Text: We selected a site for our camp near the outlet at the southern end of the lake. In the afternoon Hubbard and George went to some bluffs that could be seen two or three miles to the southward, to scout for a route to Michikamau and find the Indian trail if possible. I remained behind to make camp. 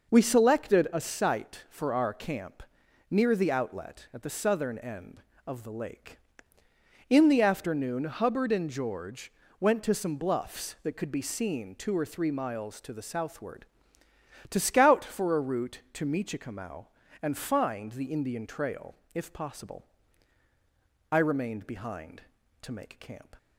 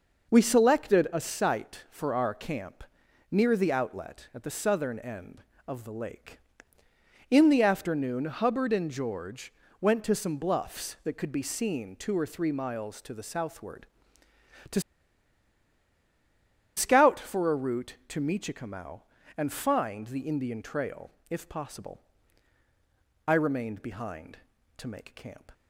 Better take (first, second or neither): first